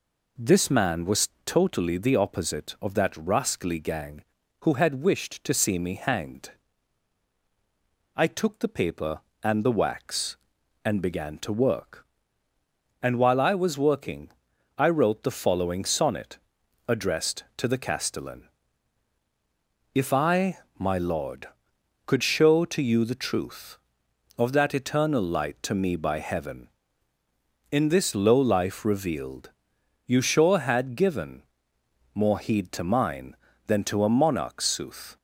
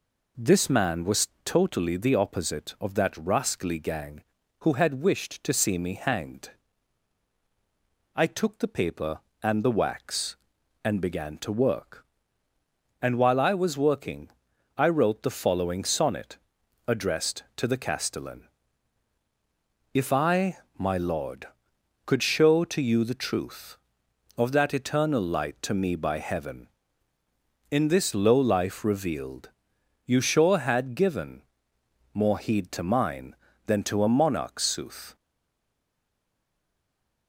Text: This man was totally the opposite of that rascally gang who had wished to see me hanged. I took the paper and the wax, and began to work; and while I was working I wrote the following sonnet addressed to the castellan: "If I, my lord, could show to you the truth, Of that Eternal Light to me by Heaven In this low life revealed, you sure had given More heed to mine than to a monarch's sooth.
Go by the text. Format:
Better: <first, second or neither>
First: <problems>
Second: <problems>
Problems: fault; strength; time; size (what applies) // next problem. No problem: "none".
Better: first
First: pauses between "was" and "totally"; slight; at 1.2 s; 0.16 s long // pauses between "working" and "I"; noticeable; at 14.3 s; 0.46 s long // pauses between "sonnet" and "addressed"; noticeable; at 16.3 s; 0.50 s long // pauses between "given" and "More"; noticeable; at 31.4 s; 0.72 s long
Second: pauses between "was" and "totally"; slight; at 1.2 s; 0.16 s long // pauses between "working" and "I"; noticeable; at 14.2 s; 0.46 s long // pauses between "sonnet" and "addressed"; noticeable; at 16.3 s; 0.50 s long // pauses between "given" and "More"; noticeable; at 31.4 s; 0.72 s long // stays silent after the last word; from 35.1 s on; 2.1 s long